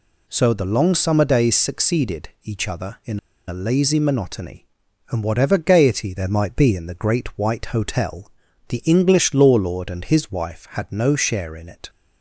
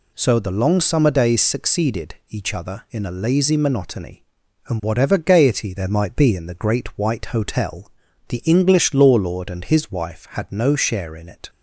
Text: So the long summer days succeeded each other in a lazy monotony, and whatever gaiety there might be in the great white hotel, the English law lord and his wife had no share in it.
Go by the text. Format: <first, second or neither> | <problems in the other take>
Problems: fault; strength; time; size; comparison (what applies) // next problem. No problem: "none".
second | pauses between "in" and "a"; slight; at 3.1 s; 0.28 s long